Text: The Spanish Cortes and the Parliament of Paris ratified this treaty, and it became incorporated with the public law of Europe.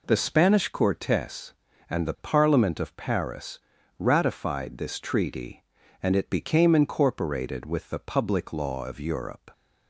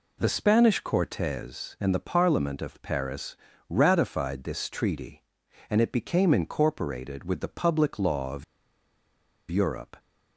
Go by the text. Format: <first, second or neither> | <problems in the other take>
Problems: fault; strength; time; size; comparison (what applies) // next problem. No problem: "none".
first | pauses between "Paris" and "ratified"; slight; at 3.3 s; 0.32 s long; also in the first // pauses between "of" and "Europe"; at 8.4 s; 1.0 s long